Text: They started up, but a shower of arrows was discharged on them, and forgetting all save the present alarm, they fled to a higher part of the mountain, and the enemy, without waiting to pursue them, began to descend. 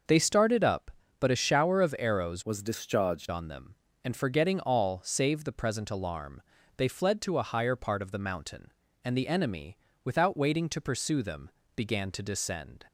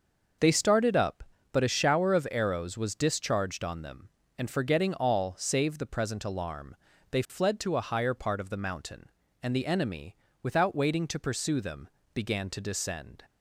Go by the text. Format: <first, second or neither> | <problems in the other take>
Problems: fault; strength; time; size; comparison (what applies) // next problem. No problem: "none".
second | starts louder than the rest; noticeable; until 1.3 s; 6 dB; noticeable in the second // changes voice from "was" to "discharged"; from 2.4 to 3.2 s; 0.8 s long